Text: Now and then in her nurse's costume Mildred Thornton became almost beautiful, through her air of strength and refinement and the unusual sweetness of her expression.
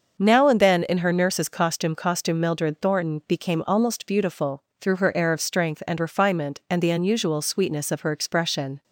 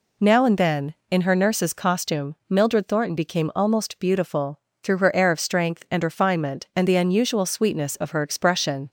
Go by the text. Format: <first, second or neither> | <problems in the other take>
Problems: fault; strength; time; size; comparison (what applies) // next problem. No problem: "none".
second | starts louder than the rest; until 1.1 s; 6.5 dB // says "costume" twice; at 1.9 s